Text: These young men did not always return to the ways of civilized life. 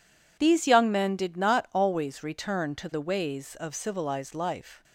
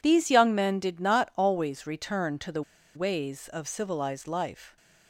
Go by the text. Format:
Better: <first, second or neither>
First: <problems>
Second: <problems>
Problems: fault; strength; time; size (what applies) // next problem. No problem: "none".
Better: first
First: none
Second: pauses between "the" and "ways"; slight; at 2.6 s; 0.34 s long